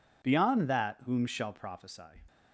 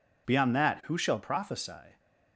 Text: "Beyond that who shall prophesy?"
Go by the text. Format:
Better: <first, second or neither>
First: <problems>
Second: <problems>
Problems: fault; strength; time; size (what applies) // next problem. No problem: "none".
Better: second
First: says "whom" for "who"; at 1.0 s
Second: none